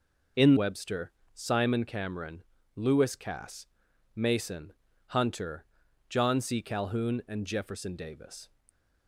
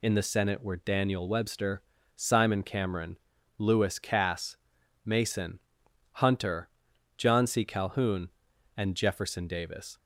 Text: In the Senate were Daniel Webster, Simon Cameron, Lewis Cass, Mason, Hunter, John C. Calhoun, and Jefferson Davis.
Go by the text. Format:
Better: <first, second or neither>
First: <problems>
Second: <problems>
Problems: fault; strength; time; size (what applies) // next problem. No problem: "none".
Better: second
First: skips "the Senate were Daniel"; at 0.5 s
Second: none